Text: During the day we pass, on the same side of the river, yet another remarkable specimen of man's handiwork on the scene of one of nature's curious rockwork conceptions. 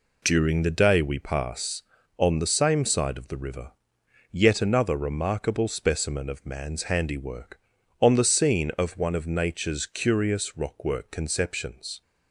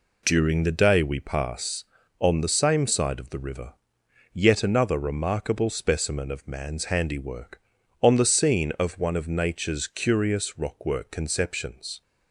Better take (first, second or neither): neither